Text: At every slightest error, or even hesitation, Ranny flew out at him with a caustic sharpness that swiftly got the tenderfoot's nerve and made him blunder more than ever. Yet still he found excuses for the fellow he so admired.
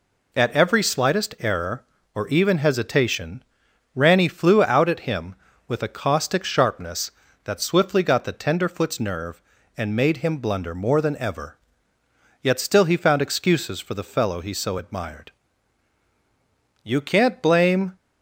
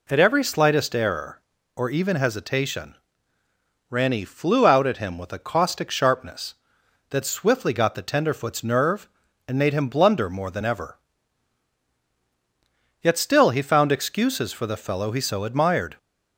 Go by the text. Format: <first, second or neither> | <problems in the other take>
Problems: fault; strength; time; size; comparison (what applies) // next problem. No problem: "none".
second | goes on to say "You can't blame"; noticeable; from 16.8 s on; 1.1 s long